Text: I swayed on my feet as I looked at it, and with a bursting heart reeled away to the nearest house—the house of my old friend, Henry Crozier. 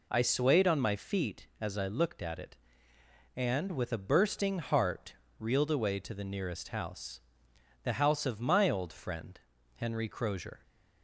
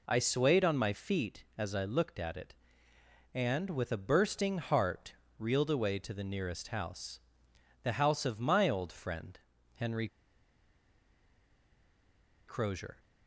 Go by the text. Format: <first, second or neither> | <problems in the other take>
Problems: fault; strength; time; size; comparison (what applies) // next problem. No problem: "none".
first | pauses between "heart" and "reeled"; slight; at 5.1 s; 0.24 s long; slight in the first // pauses between "Henry" and "Crozier"; strong; at 10.0 s; 2.3 s long